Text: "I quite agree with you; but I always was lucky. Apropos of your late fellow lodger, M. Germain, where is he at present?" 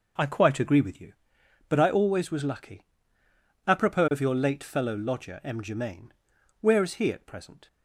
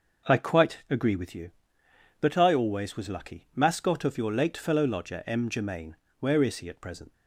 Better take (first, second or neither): first